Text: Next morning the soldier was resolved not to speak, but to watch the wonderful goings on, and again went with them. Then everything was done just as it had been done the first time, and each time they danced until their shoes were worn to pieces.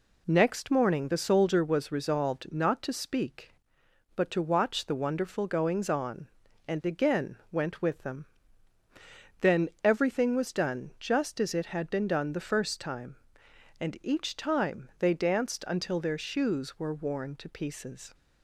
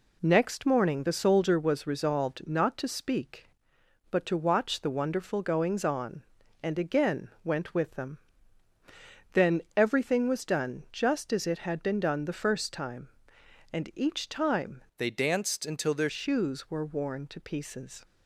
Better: first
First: pauses between "Then" and "everything"; slight; at 9.6 s; 0.16 s long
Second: pauses between "Then" and "everything"; slight; at 9.6 s; 0.16 s long // changes voice from "they" to "their"; from 14.9 to 16.0 s; 1.1 s long

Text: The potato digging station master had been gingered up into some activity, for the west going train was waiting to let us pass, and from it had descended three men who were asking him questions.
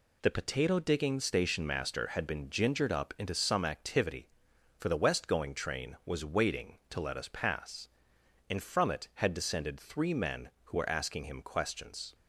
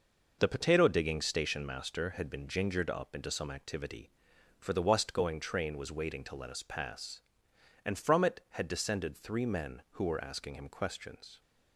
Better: neither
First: none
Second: none

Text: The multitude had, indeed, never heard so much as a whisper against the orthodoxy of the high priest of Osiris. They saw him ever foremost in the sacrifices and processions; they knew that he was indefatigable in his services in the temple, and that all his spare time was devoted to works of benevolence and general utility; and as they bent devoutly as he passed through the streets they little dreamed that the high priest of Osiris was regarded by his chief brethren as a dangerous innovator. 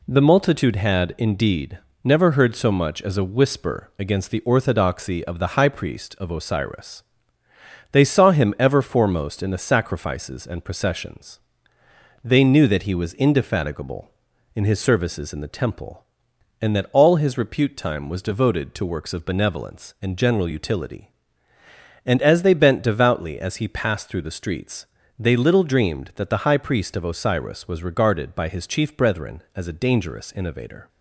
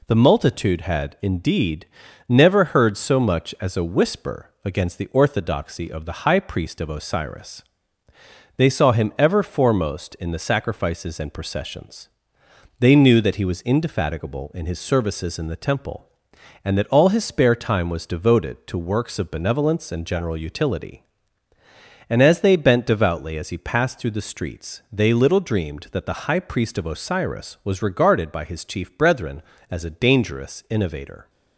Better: second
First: says "repute" for "spare"; at 17.3 s // pauses between "streets" and "they"; slight; at 24.8 s; 0.32 s long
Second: none

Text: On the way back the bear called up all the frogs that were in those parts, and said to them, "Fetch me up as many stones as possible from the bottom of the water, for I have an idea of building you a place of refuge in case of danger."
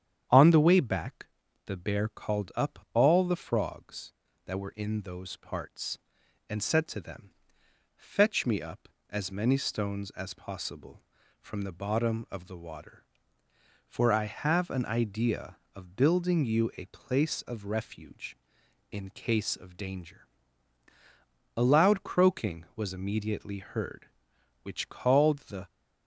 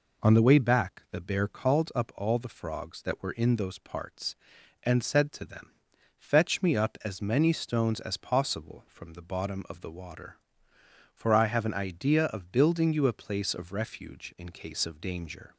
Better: second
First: starts louder than the rest; strong; until 1.6 s; 9 dB // pauses between "back" and "the"; at 1.2 s; 0.38 s long // goes on to say "A loud croaking was immediately heard which called the"; strong; from 21.5 s on; 4.1 s long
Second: none

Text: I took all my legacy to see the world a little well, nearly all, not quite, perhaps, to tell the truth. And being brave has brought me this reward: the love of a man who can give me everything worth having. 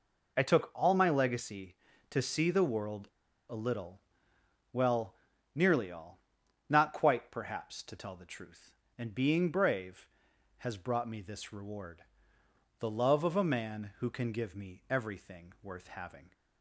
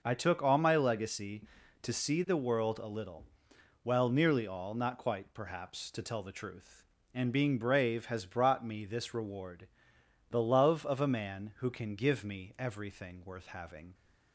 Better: second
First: pauses between "world" and "a"; at 3.0 s; 0.42 s long // pauses between "little" and "well"; noticeable; at 3.9 s; 0.76 s long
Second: pauses between "little" and "well"; noticeable; at 3.2 s; 0.58 s long

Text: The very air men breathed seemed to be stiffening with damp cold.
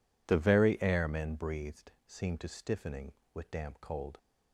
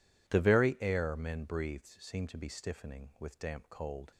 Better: second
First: pauses between "breathed" and "seemed"; slight; at 1.9 s; 0.16 s long // skips "be"; at 2.4 s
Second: none

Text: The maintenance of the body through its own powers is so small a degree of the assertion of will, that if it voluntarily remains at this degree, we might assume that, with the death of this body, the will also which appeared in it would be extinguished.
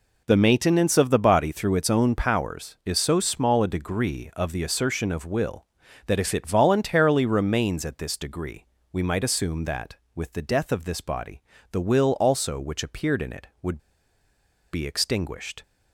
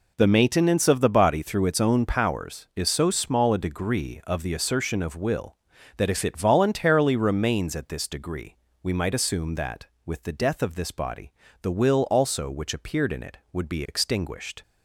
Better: second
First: pauses between "would" and "be"; noticeable; at 13.7 s; 0.95 s long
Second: none

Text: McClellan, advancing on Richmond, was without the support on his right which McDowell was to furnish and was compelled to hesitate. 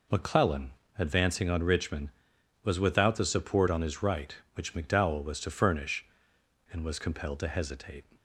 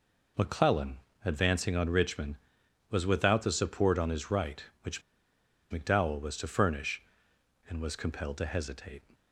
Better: first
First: none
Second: pauses between "which" and "McDowell"; noticeable; at 5.0 s; 0.69 s long

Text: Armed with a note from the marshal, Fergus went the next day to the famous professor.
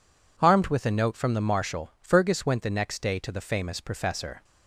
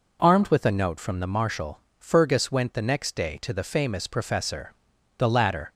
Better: first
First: none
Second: goes on to say "The latter"; from 5.1 s on; 0.54 s long

